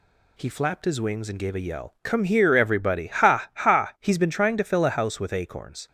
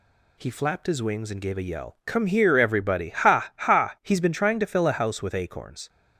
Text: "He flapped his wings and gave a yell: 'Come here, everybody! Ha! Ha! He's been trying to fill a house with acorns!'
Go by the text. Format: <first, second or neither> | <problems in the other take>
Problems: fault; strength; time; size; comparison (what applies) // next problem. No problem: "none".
neither | none